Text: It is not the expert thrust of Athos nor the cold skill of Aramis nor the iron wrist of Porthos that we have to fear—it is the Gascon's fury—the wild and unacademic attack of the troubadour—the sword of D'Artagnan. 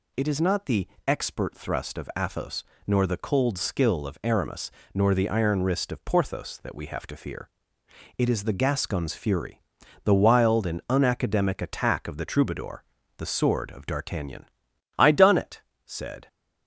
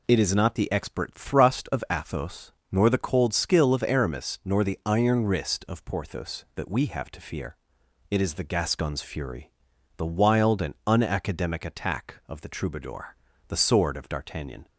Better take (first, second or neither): second